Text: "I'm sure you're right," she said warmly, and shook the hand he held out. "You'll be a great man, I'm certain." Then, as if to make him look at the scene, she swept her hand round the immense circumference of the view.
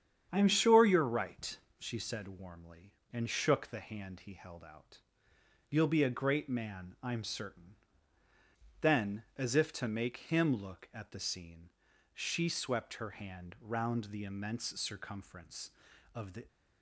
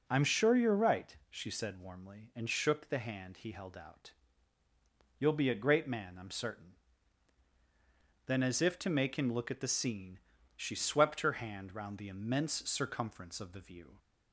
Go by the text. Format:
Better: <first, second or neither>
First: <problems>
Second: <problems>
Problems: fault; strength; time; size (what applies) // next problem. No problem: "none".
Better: second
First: starts louder than the rest; strong; until 1.3 s; 8.5 dB // stops before "view"; at 16.4 s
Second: none